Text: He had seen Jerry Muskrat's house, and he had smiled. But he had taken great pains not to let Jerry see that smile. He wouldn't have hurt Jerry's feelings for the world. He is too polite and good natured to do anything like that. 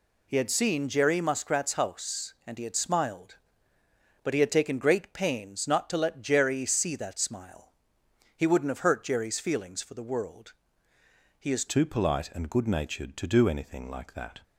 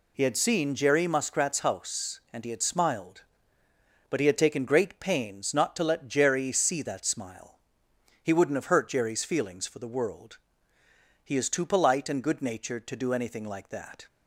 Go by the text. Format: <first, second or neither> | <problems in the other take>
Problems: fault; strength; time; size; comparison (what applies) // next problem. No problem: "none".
second | changes voice at "too"; from 11.6 s on; 2.7 s long